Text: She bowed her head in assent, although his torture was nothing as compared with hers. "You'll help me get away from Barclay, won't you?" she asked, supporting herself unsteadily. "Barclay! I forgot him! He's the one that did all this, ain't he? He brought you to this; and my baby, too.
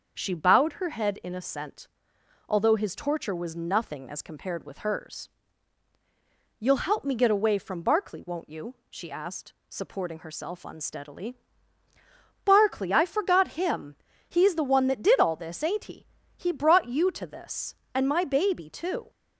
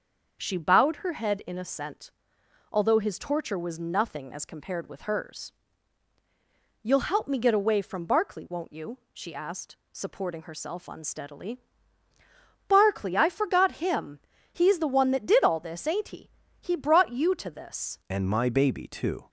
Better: first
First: starts louder than the rest; until 1.1 s; 6.5 dB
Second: starts louder than the rest; until 1.4 s; 6.5 dB // changes voice at "and"; from 18.0 s on; 1.2 s long

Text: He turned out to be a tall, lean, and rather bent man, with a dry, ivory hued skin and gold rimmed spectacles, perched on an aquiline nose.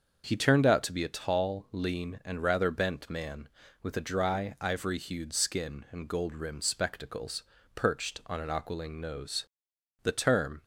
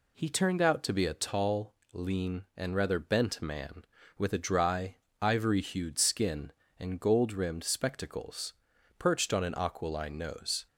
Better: second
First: starts louder than the rest; until 1.2 s; 6.5 dB // goes on to say "The term"; noticeable; from 10.0 s on; 0.62 s long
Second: none

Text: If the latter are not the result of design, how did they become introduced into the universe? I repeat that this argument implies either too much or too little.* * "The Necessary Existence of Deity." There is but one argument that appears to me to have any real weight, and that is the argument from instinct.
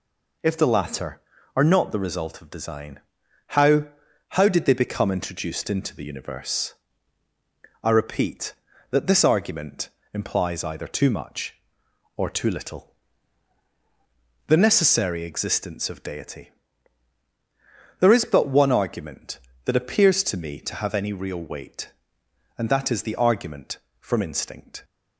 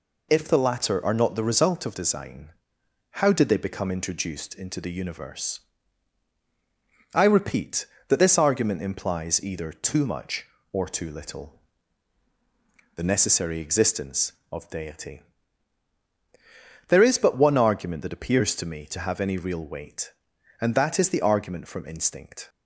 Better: second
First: says "how" twice; at 4.3 s // pauses between "argument" and "implies"; slight; at 9.8 s; 0.26 s long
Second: none

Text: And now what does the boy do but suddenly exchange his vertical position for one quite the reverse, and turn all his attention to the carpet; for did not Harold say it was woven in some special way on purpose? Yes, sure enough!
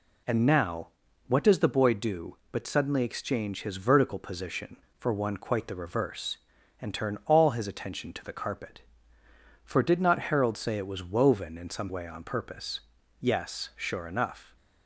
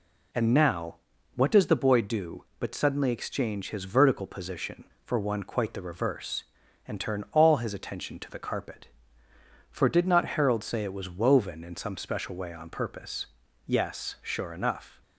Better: second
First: pauses between "now" and "what"; at 0.8 s; 0.40 s long // skips "special"; at 11.9 s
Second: pauses between "now" and "what"; at 0.9 s; 0.40 s long

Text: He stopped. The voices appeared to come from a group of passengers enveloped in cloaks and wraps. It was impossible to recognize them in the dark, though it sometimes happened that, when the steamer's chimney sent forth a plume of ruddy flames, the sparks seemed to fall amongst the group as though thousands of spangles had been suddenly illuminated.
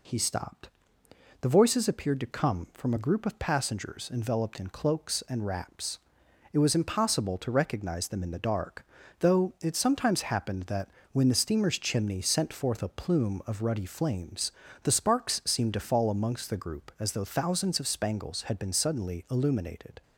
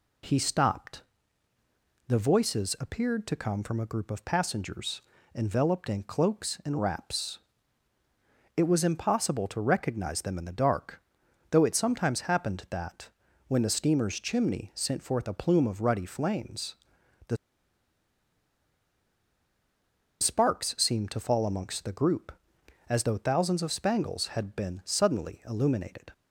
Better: first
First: none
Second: pauses between "passengers" and "enveloped"; slight; at 5.0 s; 0.32 s long // pauses between "the" and "sparks"; strong; at 17.3 s; 2.8 s long

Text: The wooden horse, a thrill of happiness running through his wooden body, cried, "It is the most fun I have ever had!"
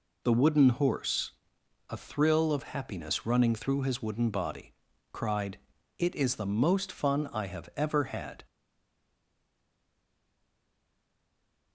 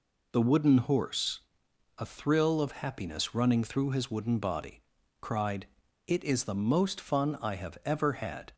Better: second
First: stays silent after the last word; strong; from 8.4 s on; 3.3 s long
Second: none

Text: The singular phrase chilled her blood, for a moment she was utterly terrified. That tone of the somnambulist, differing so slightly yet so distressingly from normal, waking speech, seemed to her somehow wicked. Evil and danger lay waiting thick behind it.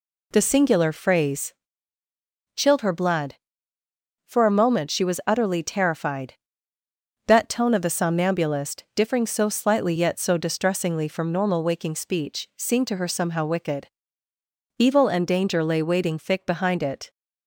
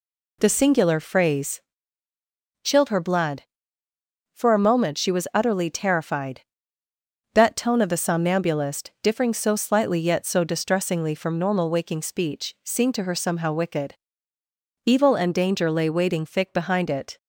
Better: neither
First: pauses between "phrase" and "chilled"; at 1.5 s; 1.0 s long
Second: pauses between "phrase" and "chilled"; at 1.5 s; 1.0 s long

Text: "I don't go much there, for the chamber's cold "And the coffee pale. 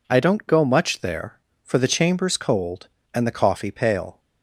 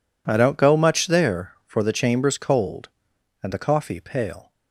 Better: neither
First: none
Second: none

